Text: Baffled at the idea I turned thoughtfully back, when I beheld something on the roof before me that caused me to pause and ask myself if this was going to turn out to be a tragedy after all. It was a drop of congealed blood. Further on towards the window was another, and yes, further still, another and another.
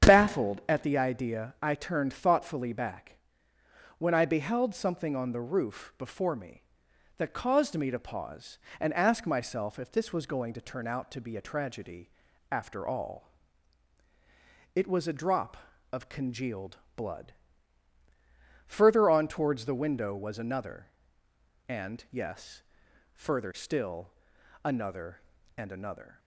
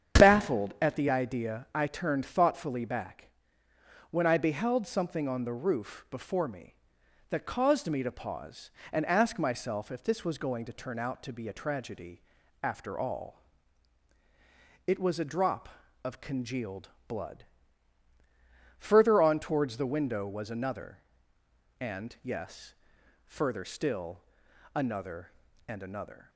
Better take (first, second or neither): neither